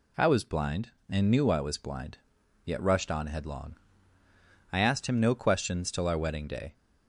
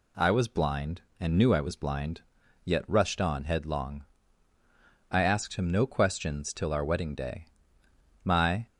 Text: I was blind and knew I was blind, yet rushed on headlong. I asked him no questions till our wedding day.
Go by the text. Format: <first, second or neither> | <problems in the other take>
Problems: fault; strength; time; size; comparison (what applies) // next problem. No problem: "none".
first | goes on to say "My"; slight; from 8.2 s on; 0.42 s long